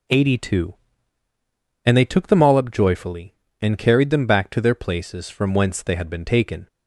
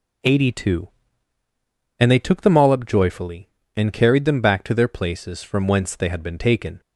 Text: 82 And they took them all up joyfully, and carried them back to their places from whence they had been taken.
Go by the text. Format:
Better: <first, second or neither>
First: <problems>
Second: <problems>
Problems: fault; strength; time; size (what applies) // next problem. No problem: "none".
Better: neither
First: none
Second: none